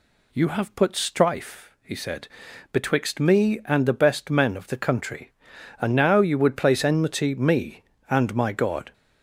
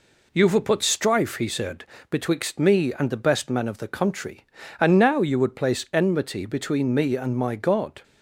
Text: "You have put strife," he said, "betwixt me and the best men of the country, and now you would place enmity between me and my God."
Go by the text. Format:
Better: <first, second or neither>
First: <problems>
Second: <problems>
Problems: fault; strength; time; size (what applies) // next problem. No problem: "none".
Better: second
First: skips "between"; at 7.3 s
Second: none